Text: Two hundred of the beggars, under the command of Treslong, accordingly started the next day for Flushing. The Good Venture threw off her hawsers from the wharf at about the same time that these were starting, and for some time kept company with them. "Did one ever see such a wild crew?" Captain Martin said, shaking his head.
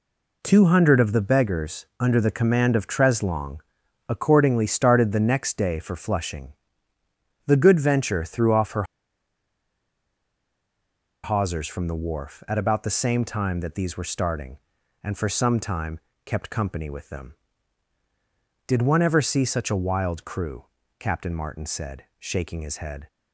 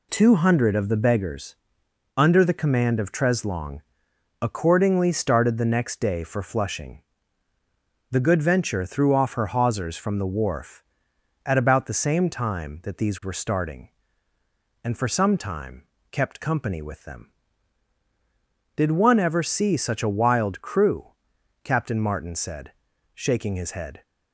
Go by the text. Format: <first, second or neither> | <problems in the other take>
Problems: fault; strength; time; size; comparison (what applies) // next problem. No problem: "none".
second | pauses between "her" and "hawsers"; strong; at 8.8 s; 2.4 s long // pauses between "time" and "kept"; slight; at 15.9 s; 0.26 s long; slight in the second